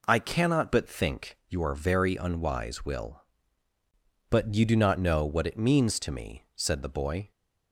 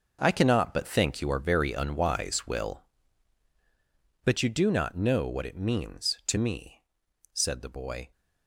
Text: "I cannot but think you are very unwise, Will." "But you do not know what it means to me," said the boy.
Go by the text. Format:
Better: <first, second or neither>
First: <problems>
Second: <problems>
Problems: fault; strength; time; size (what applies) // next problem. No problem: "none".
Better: first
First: none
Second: gets quieter; strong; throughout; 11.5 dB